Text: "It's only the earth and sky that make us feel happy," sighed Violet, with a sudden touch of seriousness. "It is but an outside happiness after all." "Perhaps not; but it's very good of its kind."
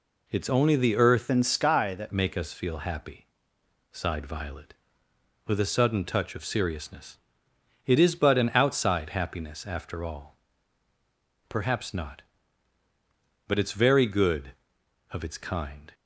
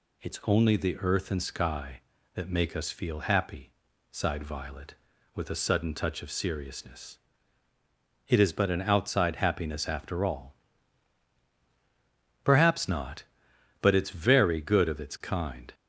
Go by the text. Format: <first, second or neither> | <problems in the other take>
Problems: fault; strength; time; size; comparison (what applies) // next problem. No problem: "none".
second | changes voice from "and" to "that"; from 1.2 to 2.1 s; 0.9 s long